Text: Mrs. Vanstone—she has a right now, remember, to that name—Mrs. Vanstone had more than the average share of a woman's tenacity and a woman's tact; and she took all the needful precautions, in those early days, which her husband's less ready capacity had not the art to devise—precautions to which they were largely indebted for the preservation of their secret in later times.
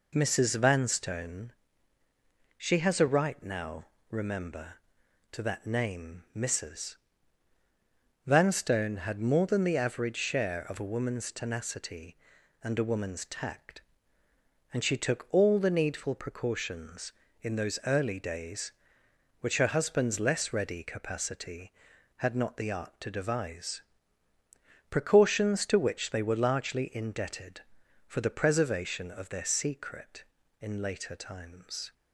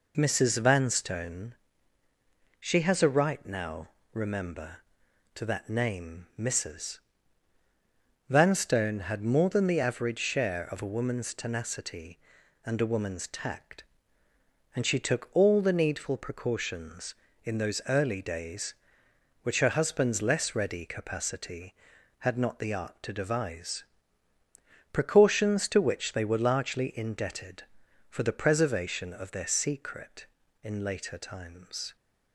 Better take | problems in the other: neither | none

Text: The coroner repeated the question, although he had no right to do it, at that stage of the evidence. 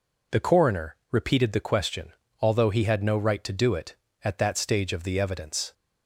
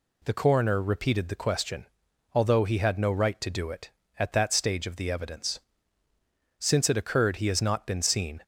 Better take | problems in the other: first | goes on to say "Since it occurred he has not been seen"; strong; from 6.5 s on; 1.8 s long

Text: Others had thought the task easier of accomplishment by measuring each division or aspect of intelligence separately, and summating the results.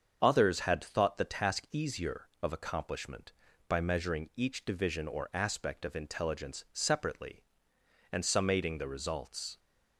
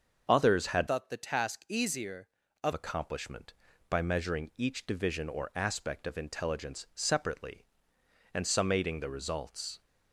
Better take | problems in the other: first | starts louder than the rest; until 1.2 s; 6.5 dB; strong in the first // changes voice from "thought" to "of"; from 0.8 to 2.7 s; 1.9 s long

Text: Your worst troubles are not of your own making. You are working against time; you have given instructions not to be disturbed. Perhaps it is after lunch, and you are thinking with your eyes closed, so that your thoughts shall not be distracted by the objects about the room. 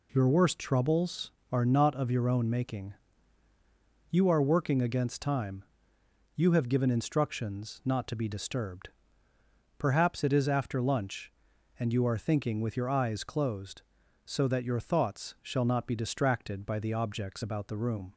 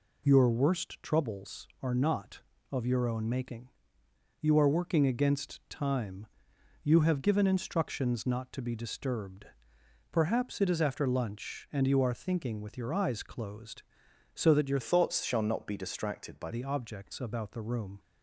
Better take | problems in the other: first | changes voice from "thoughts" to "by"; from 14.8 to 16.5 s; 1.7 s long

